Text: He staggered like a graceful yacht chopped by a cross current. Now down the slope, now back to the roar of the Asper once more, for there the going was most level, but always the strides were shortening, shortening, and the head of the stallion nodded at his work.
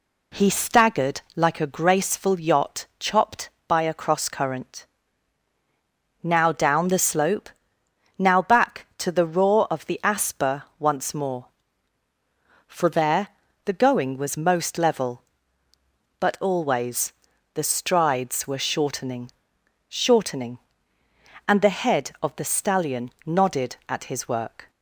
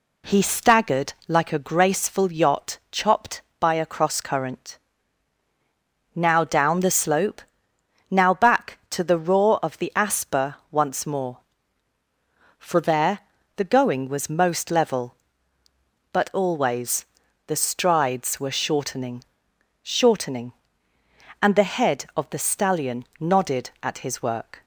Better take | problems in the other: neither | pauses between "Asper" and "once"; slight; the same in both // pauses between "there" and "the"; the same in both // pauses between "always" and "the"; the same in both // pauses between "stallion" and "nodded"; slight; the same in both

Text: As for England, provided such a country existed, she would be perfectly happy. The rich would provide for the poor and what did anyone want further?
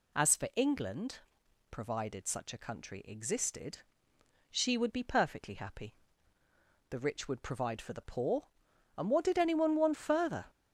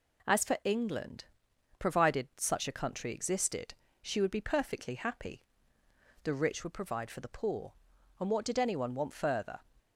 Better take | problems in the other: neither | none

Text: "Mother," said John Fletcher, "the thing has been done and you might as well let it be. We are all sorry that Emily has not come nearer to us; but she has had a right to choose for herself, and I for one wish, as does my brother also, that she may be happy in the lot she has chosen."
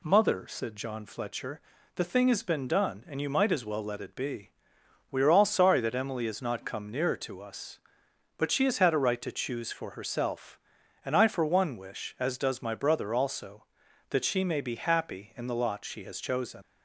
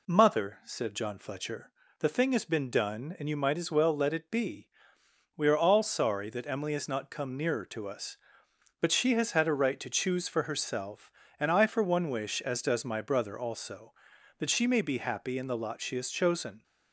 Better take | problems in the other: second | leaves "chosen" unfinished; at 16.6 s; 110 ms

